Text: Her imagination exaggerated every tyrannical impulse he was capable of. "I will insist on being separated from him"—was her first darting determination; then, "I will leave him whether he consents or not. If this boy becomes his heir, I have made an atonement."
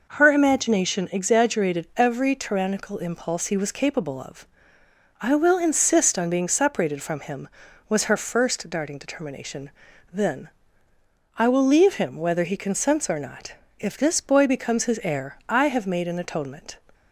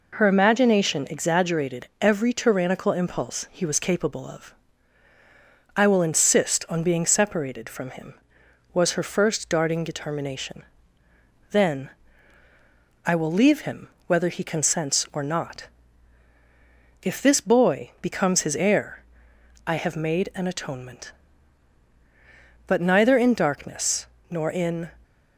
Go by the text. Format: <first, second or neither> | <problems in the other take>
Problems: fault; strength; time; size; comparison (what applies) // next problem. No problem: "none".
first | pauses between "him" and "whether"; slight; at 13.8 s; 0.18 s long // goes on to say "But neither in darkness nor in"; strong; from 22.6 s on; 2.2 s long